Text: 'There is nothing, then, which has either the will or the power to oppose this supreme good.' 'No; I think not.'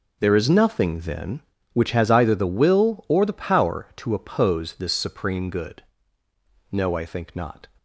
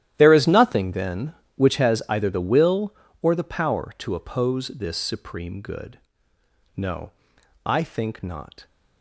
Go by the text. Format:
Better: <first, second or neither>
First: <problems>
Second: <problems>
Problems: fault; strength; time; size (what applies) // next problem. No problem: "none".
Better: first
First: none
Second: gets quieter; strong; throughout; 16.5 dB